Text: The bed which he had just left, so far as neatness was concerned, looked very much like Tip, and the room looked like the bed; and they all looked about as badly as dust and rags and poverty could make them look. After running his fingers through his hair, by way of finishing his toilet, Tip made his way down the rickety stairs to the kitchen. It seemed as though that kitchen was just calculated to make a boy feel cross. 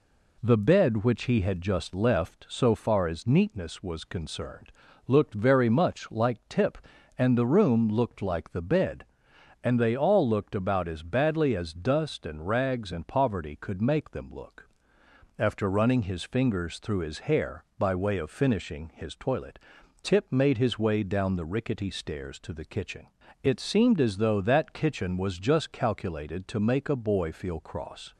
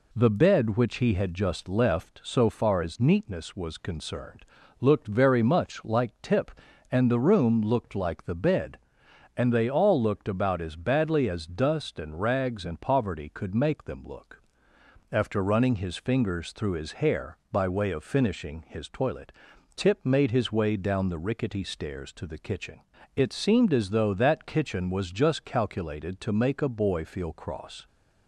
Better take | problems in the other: neither | none

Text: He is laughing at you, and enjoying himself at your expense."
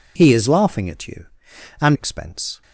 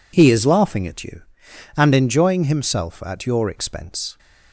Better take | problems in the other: second | skips "enjoying himself at your"; at 1.9 s

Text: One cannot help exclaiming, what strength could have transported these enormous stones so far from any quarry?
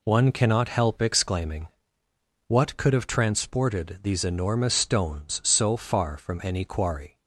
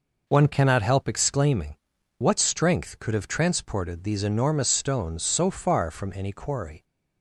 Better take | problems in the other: second | skips "strength"; at 2.7 s

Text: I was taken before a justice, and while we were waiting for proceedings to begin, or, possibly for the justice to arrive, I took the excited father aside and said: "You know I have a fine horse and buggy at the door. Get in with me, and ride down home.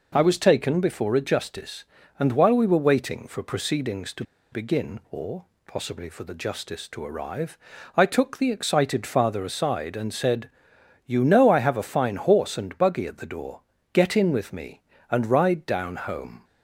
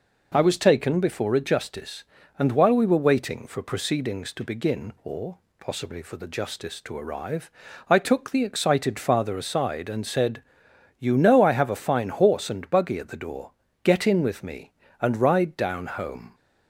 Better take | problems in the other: second | pauses between "to" and "begin"; slight; at 4.2 s; 0.28 s long

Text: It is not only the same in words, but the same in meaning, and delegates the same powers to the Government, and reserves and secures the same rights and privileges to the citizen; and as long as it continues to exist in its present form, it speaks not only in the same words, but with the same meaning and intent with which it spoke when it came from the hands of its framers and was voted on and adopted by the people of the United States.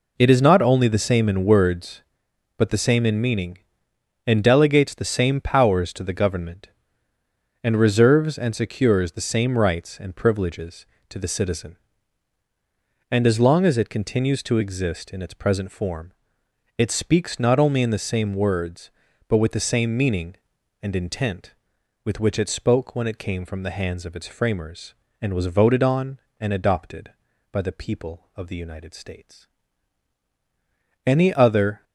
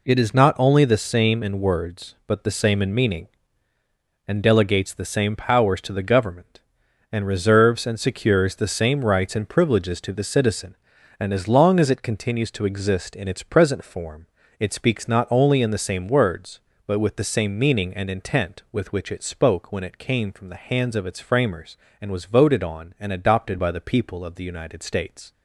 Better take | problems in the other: second | goes on to say "Any other"; noticeable; from 31.0 s on; 0.78 s long

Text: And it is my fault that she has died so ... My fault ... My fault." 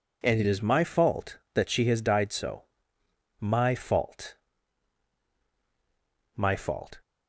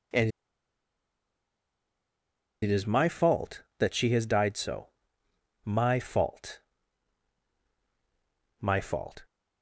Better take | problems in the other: first | pauses between "And" and "it"; strong; at 0.2 s; 2.3 s long

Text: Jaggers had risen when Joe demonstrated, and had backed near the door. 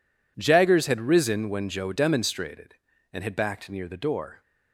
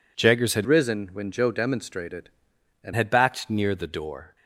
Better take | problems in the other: first | changes voice from "risen" to "and"; from 0.6 to 2.9 s; 2.3 s long

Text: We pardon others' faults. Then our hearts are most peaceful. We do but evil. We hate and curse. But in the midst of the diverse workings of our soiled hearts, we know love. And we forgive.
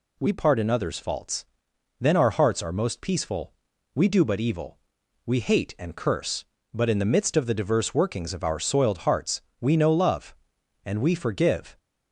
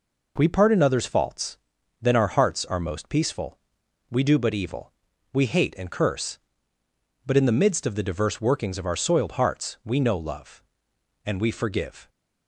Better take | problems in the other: neither | none

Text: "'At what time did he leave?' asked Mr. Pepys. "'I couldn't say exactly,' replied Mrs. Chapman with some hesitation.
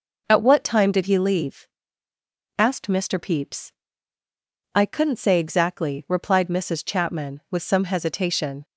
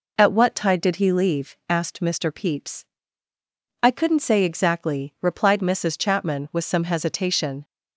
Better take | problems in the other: first | says "tide" for "time"; at 0.5 s

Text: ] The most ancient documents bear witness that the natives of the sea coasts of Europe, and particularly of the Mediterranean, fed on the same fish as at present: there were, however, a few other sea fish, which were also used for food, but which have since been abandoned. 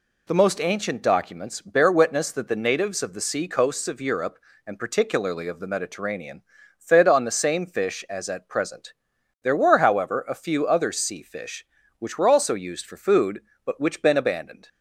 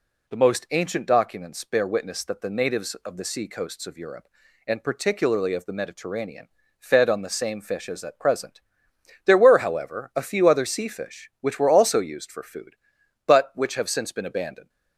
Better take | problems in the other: second | skips "have since"; at 14.0 s

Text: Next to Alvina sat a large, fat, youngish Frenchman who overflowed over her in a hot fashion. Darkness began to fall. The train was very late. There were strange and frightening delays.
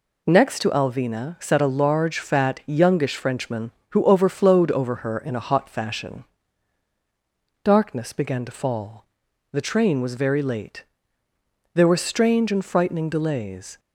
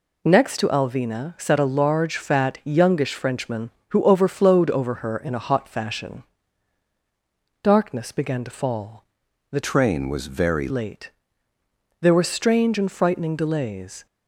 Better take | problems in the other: first | changes voice from "train" to "very"; from 9.6 to 10.6 s; 1.0 s long

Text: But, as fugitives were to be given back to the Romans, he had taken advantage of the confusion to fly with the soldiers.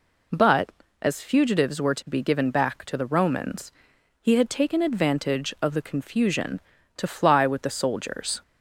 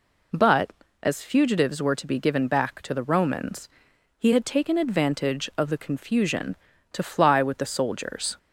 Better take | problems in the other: neither | none

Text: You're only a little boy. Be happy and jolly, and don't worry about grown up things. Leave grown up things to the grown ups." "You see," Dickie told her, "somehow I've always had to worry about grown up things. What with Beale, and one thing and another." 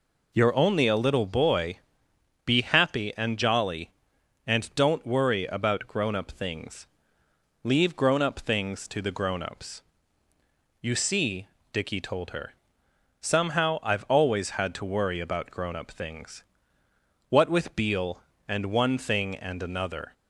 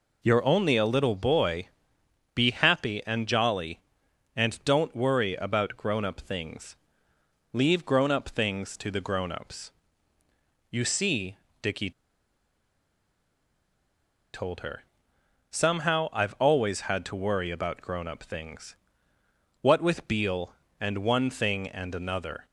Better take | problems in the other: first | pauses between "Dickie" and "told"; strong; at 11.9 s; 2.4 s long

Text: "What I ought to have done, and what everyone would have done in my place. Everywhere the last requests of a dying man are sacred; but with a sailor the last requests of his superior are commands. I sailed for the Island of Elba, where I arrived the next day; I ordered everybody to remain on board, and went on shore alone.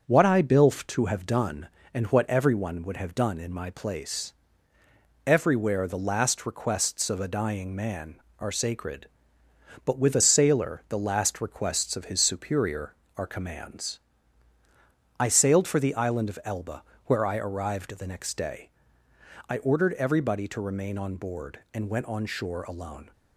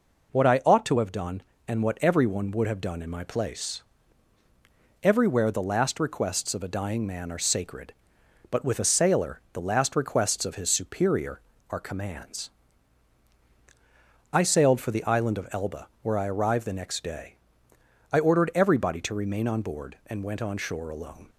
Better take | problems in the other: second | starts louder than the rest; until 1.0 s; 6.5 dB // says "bilf" for "ought"; at 0.4 s

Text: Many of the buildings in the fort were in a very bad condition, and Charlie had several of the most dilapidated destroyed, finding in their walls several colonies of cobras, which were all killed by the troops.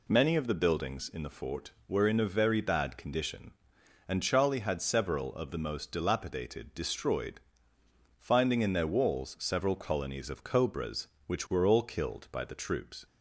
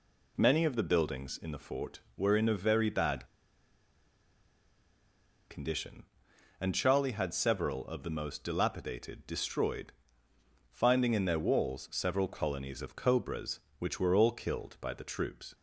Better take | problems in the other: first | pauses between "bad" and "condition"; strong; at 3.2 s; 2.2 s long

